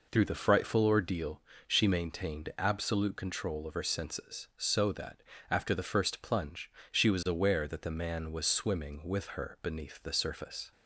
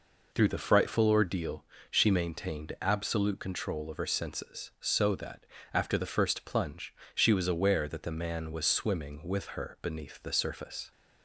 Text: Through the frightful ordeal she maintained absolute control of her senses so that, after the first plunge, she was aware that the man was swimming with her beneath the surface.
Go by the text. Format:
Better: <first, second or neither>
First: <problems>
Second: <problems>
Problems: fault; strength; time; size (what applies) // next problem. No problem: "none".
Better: neither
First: pauses between "ordeal" and "she"; slight; at 1.4 s; 0.26 s long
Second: pauses between "ordeal" and "she"; slight; at 1.6 s; 0.26 s long